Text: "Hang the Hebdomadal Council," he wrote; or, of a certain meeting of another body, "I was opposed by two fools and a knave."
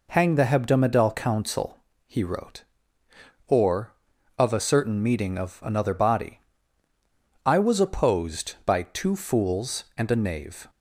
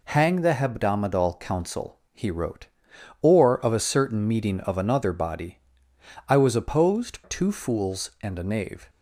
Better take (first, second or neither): first